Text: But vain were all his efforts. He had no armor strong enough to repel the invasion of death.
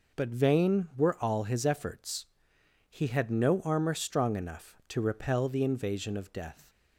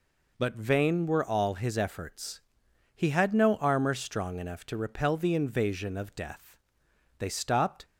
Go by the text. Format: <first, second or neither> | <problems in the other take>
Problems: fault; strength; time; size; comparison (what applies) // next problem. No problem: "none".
first | goes on to say "They stopped"; noticeable; from 7.1 s on; 0.66 s long